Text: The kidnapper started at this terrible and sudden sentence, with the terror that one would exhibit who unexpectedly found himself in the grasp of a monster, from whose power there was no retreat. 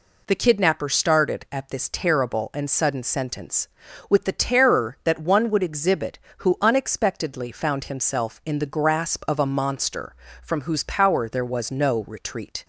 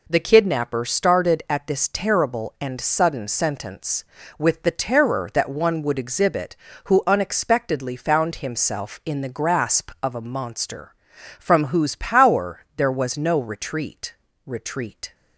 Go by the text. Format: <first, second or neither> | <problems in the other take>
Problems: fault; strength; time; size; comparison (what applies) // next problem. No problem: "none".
first | says "retreat" twice; at 14.4 s